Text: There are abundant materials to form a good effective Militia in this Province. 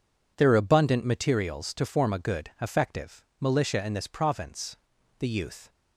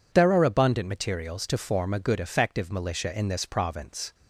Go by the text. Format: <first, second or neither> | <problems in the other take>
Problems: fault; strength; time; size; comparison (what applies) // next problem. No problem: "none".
second | goes on to say "The youth"; from 5.1 s on; 0.50 s long